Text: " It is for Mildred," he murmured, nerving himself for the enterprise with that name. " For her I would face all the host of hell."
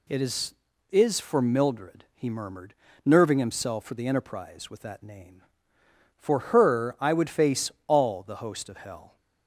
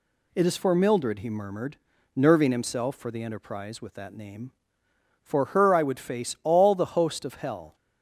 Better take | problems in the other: second | says "is" twice; at 0.8 s // pauses between "face" and "all"; slight; at 7.6 s; 0.18 s long

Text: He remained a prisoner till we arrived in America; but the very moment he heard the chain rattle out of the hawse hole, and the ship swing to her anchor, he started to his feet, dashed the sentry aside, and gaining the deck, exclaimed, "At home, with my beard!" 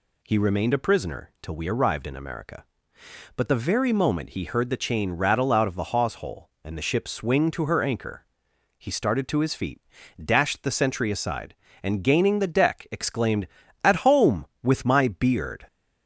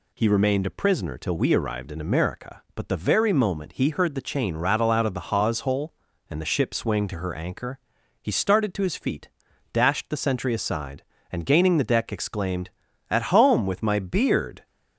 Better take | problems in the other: neither | none

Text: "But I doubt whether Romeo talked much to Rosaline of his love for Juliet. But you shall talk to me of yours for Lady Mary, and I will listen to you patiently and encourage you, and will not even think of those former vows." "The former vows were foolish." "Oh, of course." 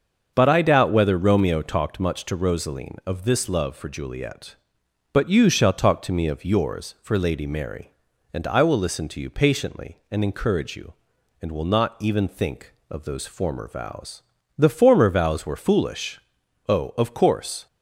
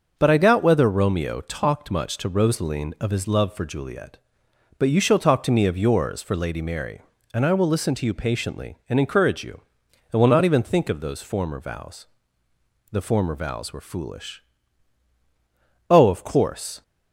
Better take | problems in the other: second | starts louder than the rest; until 1.3 s; 6.5 dB; noticeable in the second // says "this" for "his"; at 3.2 s

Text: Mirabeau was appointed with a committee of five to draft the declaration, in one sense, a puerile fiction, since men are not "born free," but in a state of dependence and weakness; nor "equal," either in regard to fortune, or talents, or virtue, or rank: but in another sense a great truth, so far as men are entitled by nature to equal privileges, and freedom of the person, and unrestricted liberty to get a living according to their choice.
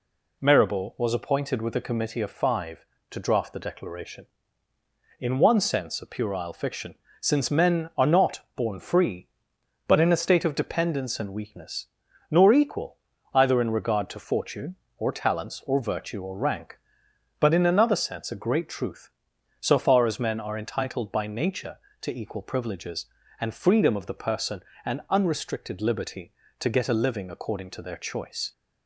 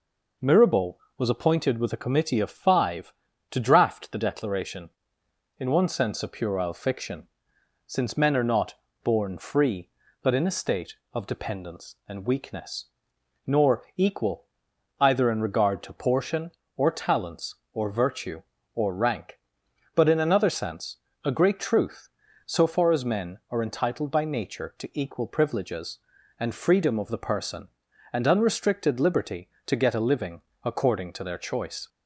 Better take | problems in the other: first | pauses between "not" and "born"; slight; at 8.7 s; 0.28 s long // says "portion" for "fortune"; at 15.9 s // pauses between "sense" and "a"; slight; at 20.9 s; 0.26 s long // pauses between "living" and "according"; slight; at 30.4 s; 0.22 s long

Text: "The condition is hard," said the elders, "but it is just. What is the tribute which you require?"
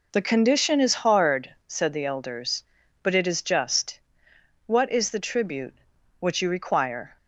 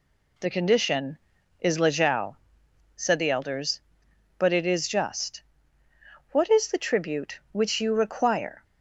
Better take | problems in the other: first | says "lejao" for "hard"; at 1.7 s

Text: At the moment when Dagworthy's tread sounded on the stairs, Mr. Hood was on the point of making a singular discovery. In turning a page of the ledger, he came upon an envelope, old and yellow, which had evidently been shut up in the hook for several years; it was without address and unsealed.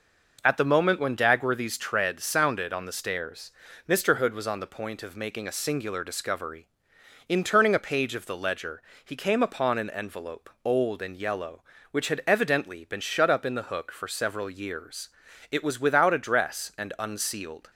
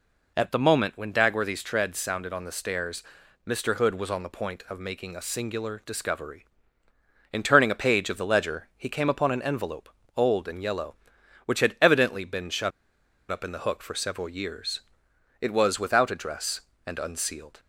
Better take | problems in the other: first | pauses between "shut" and "up"; noticeable; at 12.7 s; 0.60 s long

